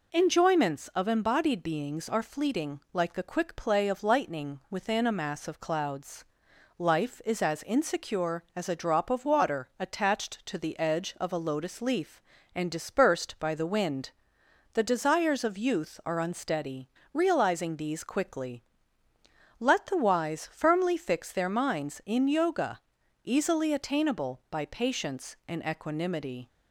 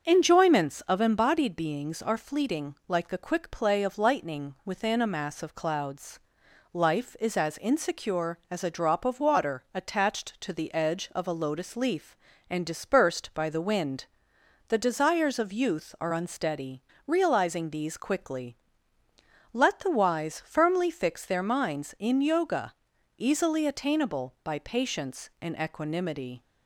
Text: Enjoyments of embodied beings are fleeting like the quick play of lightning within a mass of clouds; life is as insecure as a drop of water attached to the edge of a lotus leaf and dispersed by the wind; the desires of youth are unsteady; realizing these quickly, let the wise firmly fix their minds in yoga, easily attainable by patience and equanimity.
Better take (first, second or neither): first